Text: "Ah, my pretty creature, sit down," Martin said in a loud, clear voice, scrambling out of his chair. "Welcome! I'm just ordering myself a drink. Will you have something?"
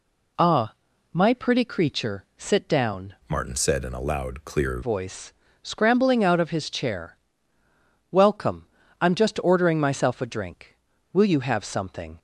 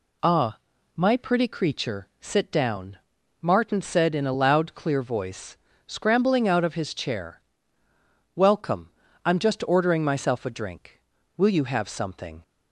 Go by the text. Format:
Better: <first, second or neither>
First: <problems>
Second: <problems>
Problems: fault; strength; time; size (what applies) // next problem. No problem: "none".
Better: second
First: changes voice from "Martin" to "clear"; from 3.2 to 4.8 s; 1.6 s long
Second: none